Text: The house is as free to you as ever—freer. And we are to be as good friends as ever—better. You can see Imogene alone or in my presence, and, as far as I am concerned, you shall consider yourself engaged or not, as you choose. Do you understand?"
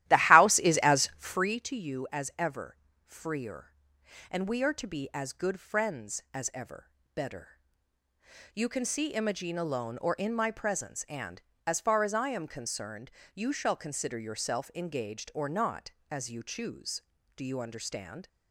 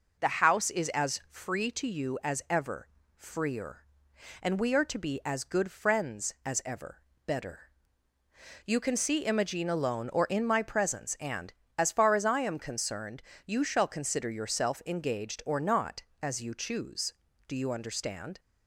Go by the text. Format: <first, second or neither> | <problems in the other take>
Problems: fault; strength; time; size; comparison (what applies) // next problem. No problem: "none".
second | starts louder than the rest; strong; until 1.5 s; 14 dB